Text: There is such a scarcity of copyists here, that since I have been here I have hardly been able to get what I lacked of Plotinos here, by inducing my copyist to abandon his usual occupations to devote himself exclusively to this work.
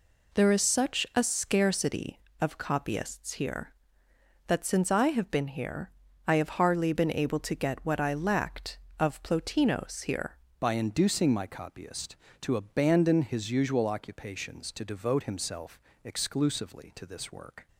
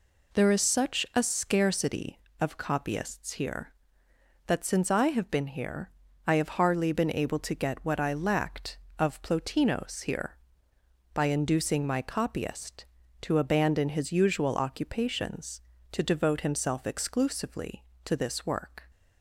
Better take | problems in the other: second | pauses between "here" and "I"; slight; at 5.8 s; 0.36 s long; slight in the second // changes voice at "by"; from 10.6 s on; 7.0 s long // pauses between "himself" and "exclusively"; slight; at 15.7 s; 0.24 s long

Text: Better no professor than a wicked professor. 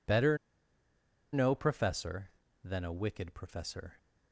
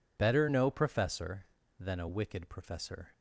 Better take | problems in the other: second | pauses between "Better" and "no"; noticeable; at 0.3 s; 0.96 s long

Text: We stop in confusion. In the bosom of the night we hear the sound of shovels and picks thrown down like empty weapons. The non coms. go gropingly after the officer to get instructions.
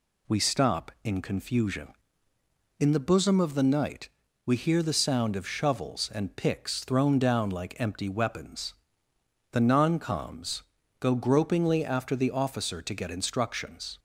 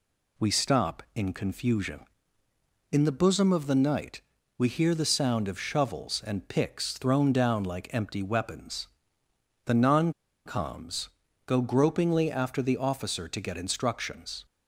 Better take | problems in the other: first | pauses between "night" and "we"; at 4.2 s; 0.38 s long; also in the first // pauses between "non" and "coms"; slight; at 10.1 s; 0.33 s long

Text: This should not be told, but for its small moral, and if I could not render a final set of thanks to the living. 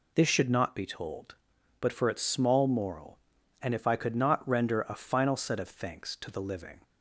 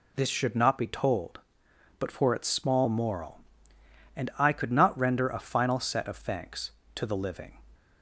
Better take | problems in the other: first | skips "if"; at 4.3 s

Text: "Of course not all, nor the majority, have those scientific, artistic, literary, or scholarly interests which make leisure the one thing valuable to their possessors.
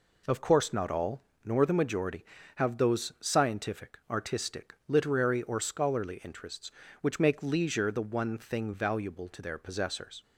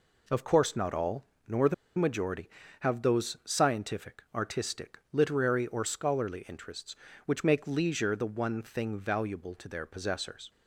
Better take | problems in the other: first | pauses between "the" and "majority"; slight; at 1.7 s; 0.23 s long

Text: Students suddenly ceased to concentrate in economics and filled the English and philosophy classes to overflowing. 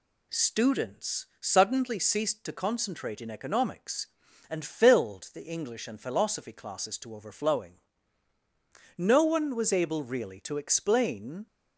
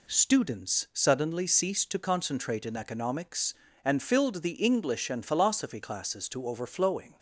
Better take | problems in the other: second | goes on to say "No one was able really to explain"; strong; from 8.9 s on; 2.5 s long

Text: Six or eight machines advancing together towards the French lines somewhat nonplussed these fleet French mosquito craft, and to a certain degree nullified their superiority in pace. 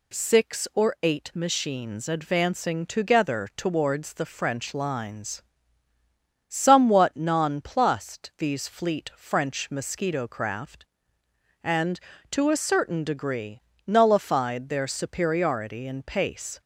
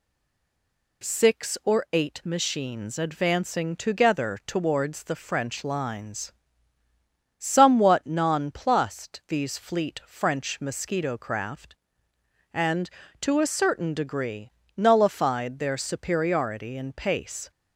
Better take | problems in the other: first | stays silent before the first word; until 1.0 s; 1.0 s long // pauses between "lines" and "somewhat"; at 6.3 s; 1.0 s long; also in the first // pauses between "degree" and "nullified"; slight; at 14.5 s; 0.24 s long; slight in the first

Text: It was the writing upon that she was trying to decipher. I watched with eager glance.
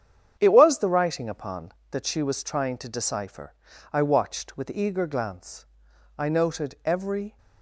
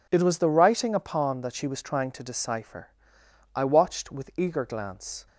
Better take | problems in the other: second | starts louder than the rest; strong; until 1.4 s; 8 dB // goes on to say "I noted every"; noticeable; from 6.1 s on; 1.2 s long

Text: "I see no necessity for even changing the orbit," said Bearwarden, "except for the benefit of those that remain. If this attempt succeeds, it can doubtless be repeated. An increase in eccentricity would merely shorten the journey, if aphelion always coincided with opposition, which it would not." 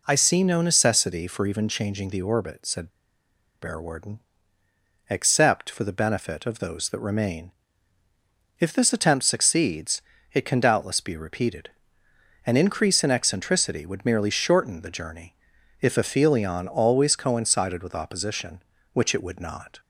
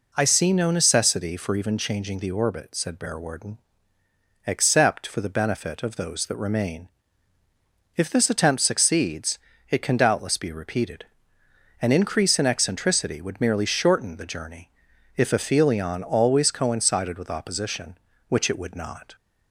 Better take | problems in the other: second | pauses between "said" and "Bearwarden"; noticeable; at 2.8 s; 0.72 s long

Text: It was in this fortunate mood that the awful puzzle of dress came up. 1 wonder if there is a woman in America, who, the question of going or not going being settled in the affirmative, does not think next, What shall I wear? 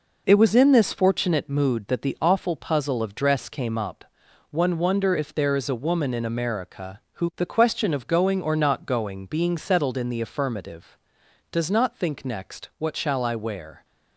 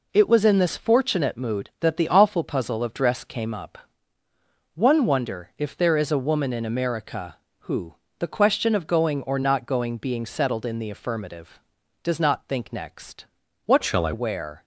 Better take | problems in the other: first | changes voice from "shall" to "I"; from 13.8 to 14.1 s; 0.3 s long

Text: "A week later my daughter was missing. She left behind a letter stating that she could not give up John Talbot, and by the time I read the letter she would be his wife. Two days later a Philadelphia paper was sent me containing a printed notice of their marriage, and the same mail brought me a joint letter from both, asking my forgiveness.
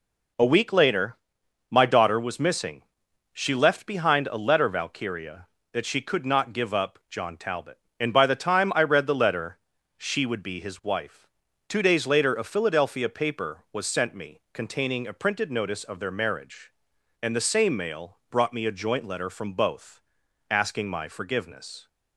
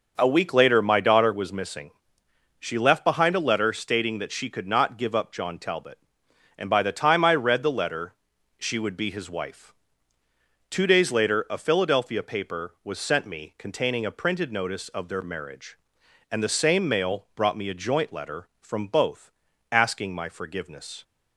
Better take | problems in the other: second | pauses between "later" and "my"; noticeable; at 1.1 s; 0.54 s long // says "valkyria" for "stating"; at 4.6 s // pauses between "letter" and "she"; at 9.5 s; 0.38 s long; also in the second

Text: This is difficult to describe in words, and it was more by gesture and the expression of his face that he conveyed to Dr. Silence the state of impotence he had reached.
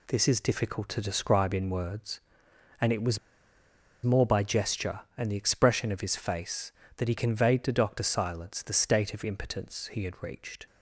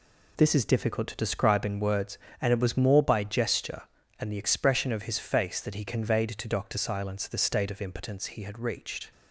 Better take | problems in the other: second | pauses between "was" and "more"; noticeable; at 3.1 s; 0.85 s long

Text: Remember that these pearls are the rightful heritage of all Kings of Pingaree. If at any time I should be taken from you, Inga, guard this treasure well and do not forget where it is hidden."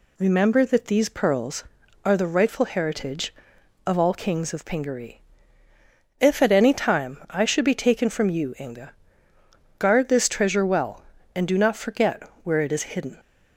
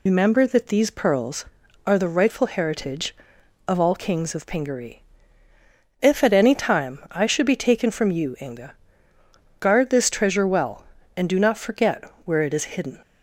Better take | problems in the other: first | loses the start of "Remember"; at 0.0 s; 65 ms // pauses between "forget" and "where"; slight; at 12.0 s; 0.22 s long; slight in the first

